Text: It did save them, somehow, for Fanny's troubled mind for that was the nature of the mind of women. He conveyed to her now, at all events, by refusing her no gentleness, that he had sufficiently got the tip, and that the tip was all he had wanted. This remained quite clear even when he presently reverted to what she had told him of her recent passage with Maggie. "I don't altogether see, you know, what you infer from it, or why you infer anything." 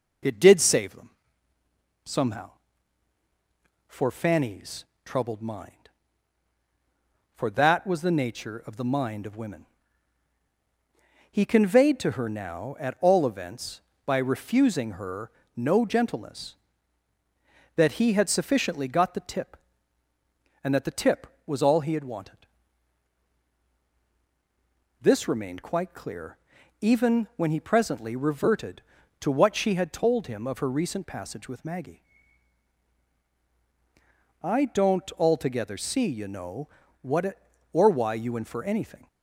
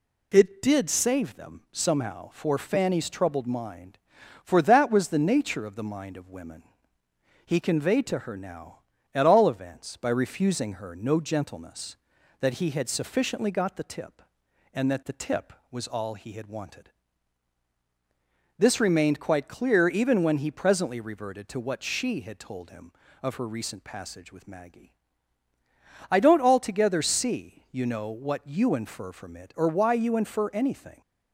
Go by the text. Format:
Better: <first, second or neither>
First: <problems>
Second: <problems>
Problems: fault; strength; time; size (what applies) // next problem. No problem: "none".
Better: second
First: pauses between "Fanny's" and "troubled"; slight; at 4.8 s; 0.18 s long // pauses between "her" and "no"; slight; at 15.3 s; 0.24 s long // pauses between "clear" and "even"; at 26.3 s; 0.42 s long // skips "you infer from"; at 37.2 s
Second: none